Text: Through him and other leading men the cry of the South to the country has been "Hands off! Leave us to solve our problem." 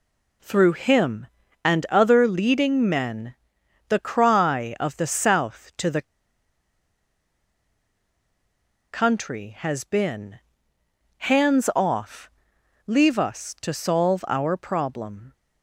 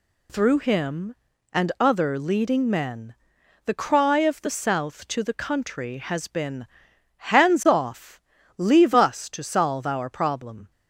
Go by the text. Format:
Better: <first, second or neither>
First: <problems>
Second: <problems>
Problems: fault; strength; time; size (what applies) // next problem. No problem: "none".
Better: second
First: pauses between "men" and "the"; noticeable; at 3.3 s; 0.54 s long // pauses between "the" and "country"; strong; at 6.0 s; 2.8 s long // pauses between "been" and "Hands"; noticeable; at 10.3 s; 0.80 s long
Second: pauses between "men" and "the"; noticeable; at 3.1 s; 0.50 s long // pauses between "been" and "Hands"; noticeable; at 6.6 s; 0.66 s long